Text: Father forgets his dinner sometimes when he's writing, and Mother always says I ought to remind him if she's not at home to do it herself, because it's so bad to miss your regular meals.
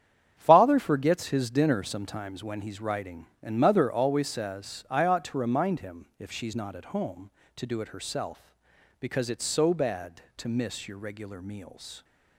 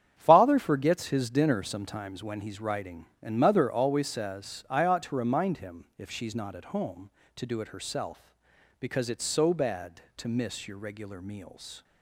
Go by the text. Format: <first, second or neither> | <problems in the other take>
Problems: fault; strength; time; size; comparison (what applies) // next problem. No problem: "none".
neither | starts louder than the rest; strong; the same in both